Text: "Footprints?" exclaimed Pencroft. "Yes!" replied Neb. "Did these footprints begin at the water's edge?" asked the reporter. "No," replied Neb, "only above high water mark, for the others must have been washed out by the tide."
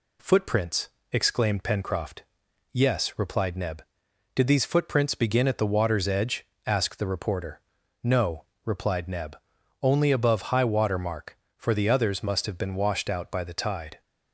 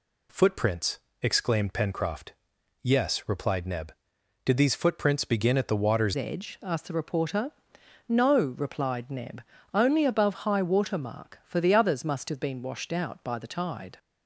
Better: first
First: none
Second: changes voice at "edge"; from 6.1 s on; 7.8 s long

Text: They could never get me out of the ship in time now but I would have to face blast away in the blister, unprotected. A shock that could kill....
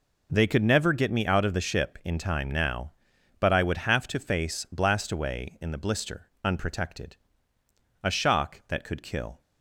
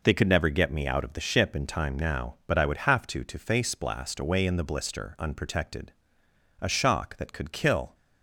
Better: first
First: none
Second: says "to" twice; at 3.2 s

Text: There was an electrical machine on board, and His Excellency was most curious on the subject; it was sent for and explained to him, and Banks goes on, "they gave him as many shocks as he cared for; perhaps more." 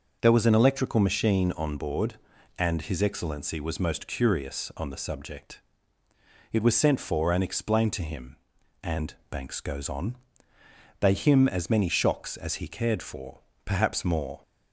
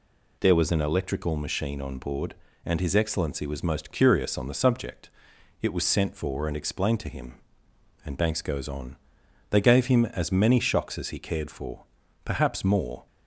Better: second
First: pauses between "and" and "Banks"; slight; at 9.1 s; 0.16 s long // skips "gave"; at 11.1 s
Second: none

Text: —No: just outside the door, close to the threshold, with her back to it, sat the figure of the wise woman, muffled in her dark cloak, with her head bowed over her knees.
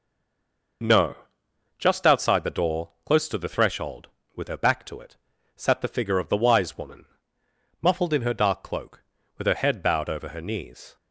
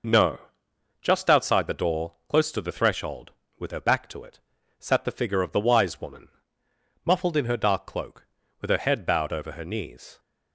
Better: second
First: stays silent before the first word; slight; until 0.8 s; 0.8 s long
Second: none

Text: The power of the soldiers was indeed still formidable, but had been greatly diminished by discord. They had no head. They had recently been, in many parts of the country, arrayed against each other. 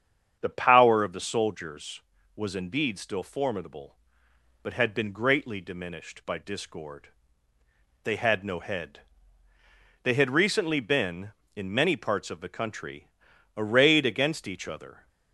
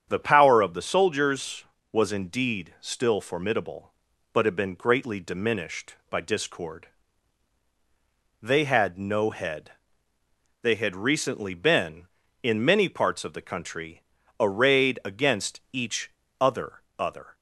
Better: first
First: starts louder than the rest; strong; until 1.4 s; 8 dB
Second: starts louder than the rest; strong; until 1.1 s; 8 dB // pauses between "each" and "other"; slight; at 16.0 s; 0.30 s long // says "other" twice; at 16.9 s

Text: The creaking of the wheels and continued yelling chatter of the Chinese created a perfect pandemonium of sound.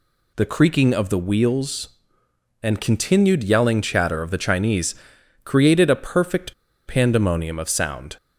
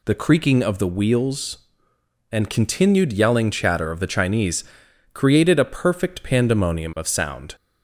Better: second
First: pauses between "Chinese" and "created"; noticeable; at 4.9 s; 0.48 s long // pauses between "perfect" and "pandemonium"; slight; at 6.5 s; 0.34 s long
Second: pauses between "Chinese" and "created"; noticeable; at 4.6 s; 0.48 s long

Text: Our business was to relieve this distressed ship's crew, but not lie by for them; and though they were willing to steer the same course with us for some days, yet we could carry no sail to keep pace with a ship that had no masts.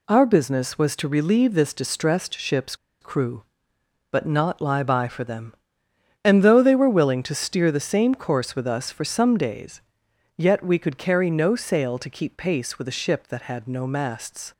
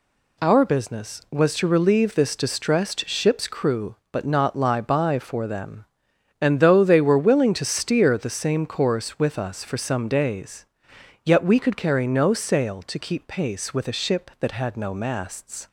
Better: second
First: pauses between "ship's" and "crew"; slight; at 2.7 s; 0.26 s long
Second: none

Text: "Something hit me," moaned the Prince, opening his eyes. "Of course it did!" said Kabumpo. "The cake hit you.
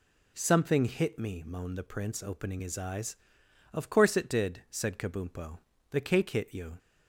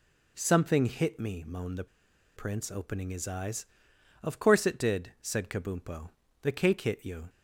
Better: first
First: none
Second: pauses between "the" and "Prince"; noticeable; at 1.8 s; 0.52 s long

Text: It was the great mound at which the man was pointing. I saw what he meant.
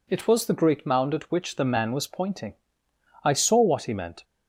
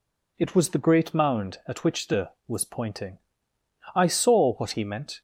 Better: first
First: none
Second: skips "man"; at 2.3 s

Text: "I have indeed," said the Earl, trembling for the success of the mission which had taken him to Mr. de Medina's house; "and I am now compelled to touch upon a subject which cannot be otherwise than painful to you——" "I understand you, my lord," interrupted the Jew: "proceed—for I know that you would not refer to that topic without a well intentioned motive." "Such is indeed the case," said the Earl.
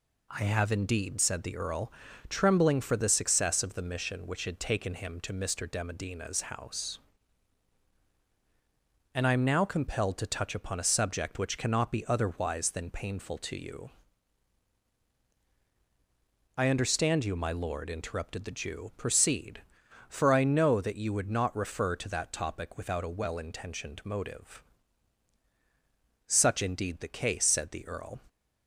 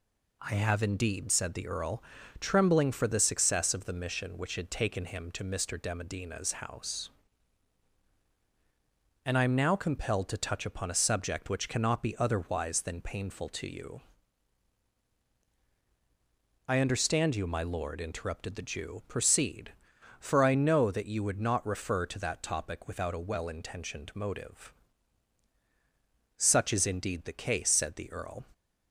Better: second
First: skips "is"; at 26.6 s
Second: none

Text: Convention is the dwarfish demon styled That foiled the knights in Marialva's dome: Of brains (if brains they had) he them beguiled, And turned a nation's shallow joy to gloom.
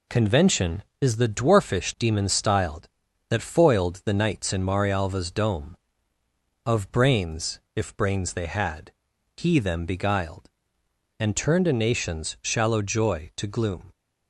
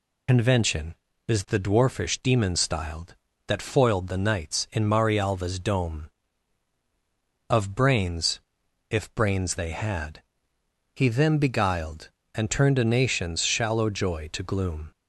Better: first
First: none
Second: loses the start of "Convention"; at 0.2 s; 65 ms

